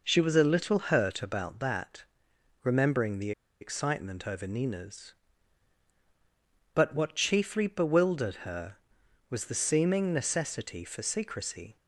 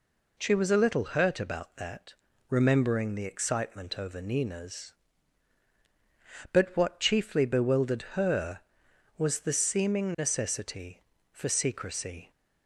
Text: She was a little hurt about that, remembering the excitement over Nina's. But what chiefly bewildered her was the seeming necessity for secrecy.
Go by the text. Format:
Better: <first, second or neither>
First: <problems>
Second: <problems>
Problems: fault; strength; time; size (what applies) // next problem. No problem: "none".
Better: second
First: pauses between "the" and "excitement"; slight; at 3.3 s; 0.30 s long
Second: none